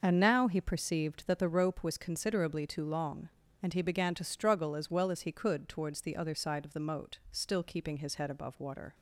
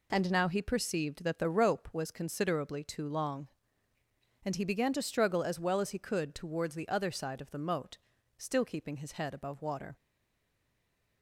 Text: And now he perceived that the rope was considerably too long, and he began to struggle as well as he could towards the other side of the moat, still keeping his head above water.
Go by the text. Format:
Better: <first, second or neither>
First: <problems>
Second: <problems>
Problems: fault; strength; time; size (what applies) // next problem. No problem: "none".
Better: first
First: none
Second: stays silent after the last word; noticeable; from 9.9 s on; 1.3 s long